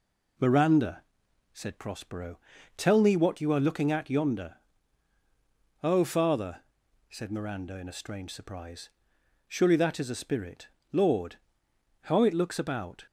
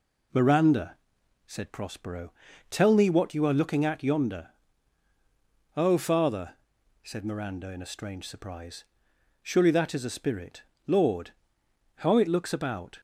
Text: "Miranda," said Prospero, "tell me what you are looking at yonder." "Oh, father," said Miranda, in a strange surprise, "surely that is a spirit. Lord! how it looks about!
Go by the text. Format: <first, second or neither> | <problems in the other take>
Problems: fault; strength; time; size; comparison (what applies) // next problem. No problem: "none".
neither | none